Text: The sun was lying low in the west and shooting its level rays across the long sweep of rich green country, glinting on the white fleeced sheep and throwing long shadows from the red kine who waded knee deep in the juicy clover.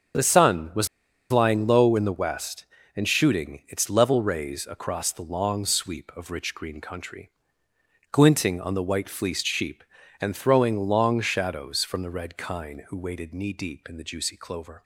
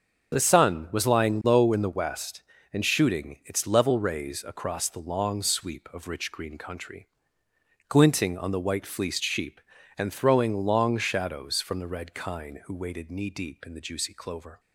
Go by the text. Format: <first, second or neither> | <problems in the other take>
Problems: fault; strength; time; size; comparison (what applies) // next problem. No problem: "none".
second | starts louder than the rest; until 1.6 s; 7 dB; strong in the second // pauses between "was" and "lying"; at 0.8 s; 0.42 s long